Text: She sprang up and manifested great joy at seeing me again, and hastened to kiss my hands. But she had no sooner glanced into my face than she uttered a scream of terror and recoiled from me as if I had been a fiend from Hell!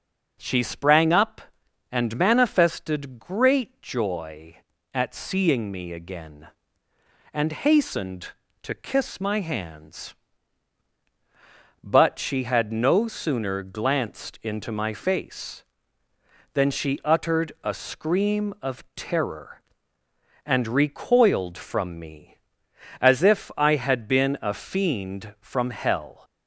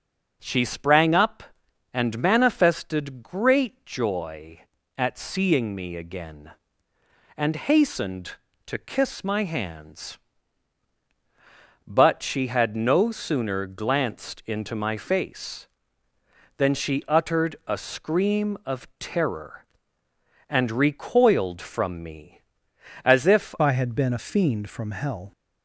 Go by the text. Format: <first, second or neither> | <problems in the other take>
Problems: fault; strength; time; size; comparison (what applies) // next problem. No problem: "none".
first | changes voice at "I"; from 23.5 s on; 1.8 s long